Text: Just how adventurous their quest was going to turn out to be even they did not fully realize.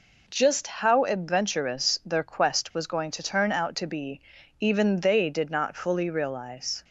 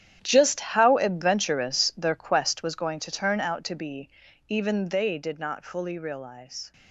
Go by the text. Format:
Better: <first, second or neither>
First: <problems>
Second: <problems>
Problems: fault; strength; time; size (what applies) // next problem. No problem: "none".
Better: first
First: pauses between "be" and "even"; at 4.1 s; 0.40 s long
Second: gets quieter; strong; throughout; 14 dB // pauses between "be" and "even"; at 4.0 s; 0.40 s long